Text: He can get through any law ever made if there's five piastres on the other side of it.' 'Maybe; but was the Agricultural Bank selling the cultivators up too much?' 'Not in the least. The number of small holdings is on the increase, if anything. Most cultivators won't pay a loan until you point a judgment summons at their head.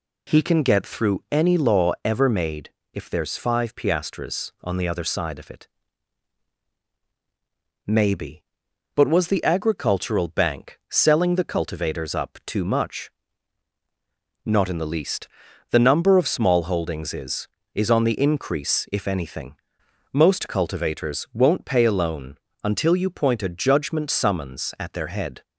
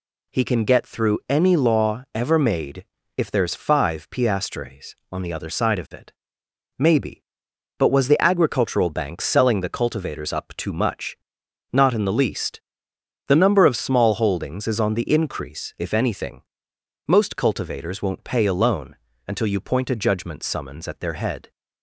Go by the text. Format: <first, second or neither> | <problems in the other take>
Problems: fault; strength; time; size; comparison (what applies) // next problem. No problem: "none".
second | pauses between "made" and "if"; slight; at 2.6 s; 0.24 s long; slight in the second // says "is" twice; at 17.7 s // pauses between "loan" and "until"; slight; at 22.3 s; 0.28 s long; slight in the second